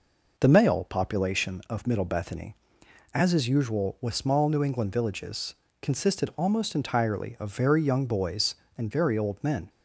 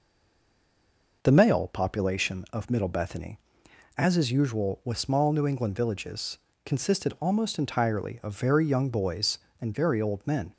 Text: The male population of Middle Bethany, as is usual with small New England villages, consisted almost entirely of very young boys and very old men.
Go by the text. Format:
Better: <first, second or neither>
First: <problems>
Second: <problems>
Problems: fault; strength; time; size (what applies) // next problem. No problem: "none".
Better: first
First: none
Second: stays silent before the first word; noticeable; until 1.2 s; 1.2 s long